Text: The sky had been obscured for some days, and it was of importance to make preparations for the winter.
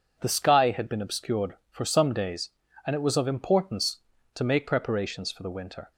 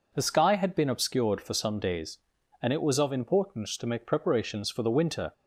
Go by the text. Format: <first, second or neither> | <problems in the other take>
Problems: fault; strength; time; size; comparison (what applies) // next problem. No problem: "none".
neither | none